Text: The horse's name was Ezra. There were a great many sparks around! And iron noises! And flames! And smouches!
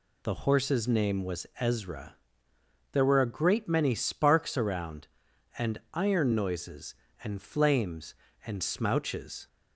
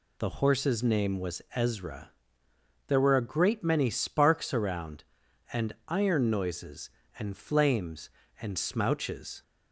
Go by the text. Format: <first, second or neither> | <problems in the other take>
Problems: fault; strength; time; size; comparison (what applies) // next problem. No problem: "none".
neither | pauses between "And" and "iron"; slight; the same in both